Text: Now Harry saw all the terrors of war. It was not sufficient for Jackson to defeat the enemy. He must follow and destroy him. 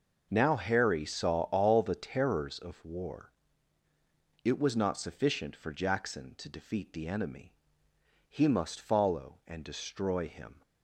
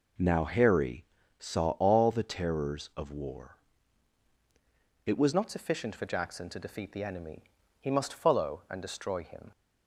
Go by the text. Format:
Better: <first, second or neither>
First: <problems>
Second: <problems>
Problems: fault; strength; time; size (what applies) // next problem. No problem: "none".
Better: first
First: none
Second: pauses between "Harry" and "saw"; slight; at 1.0 s; 0.34 s long // changes voice at "not"; from 5.3 s on; 4.2 s long